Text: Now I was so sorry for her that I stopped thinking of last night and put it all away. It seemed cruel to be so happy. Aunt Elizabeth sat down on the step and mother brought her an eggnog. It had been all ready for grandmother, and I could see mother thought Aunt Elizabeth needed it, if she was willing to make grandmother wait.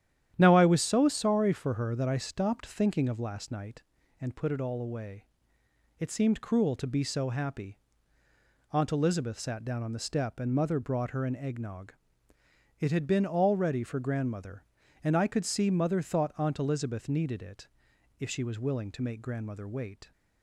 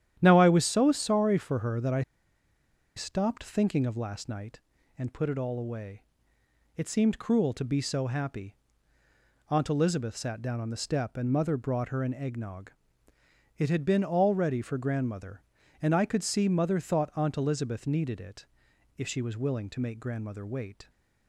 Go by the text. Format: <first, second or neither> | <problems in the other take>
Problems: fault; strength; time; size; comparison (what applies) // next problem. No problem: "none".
first | starts louder than the rest; strong; until 1.1 s; 10.5 dB; strong in the first // pauses between "I" and "stopped"; noticeable; at 2.0 s; 0.95 s long